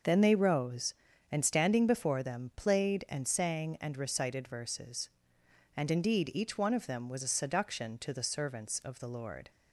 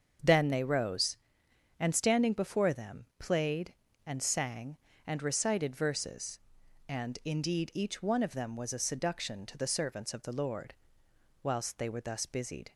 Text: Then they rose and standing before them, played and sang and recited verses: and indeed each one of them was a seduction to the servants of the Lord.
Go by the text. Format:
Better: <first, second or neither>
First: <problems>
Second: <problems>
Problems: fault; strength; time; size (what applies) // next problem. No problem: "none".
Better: first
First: none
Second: starts louder than the rest; until 1.8 s; 7 dB // goes on to say "Whilst they were thus busied"; noticeable; from 11.4 s on; 1.3 s long